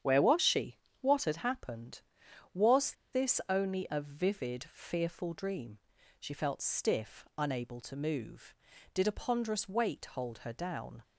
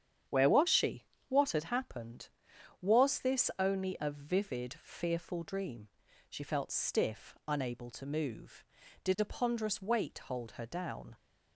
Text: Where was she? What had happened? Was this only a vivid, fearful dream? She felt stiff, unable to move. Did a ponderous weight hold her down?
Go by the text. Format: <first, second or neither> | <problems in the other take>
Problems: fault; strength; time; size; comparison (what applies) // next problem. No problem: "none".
second | starts louder than the rest; strong; until 1.2 s; 8.5 dB; strong in the second // pauses between "Was" and "this"; slight; at 2.9 s; 0.20 s long